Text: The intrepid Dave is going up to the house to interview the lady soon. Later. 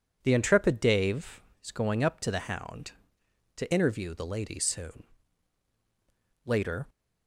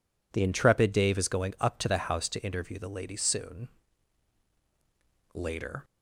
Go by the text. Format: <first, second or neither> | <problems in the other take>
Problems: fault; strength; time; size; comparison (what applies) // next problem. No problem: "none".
second | says "hound" for "house"; at 2.4 s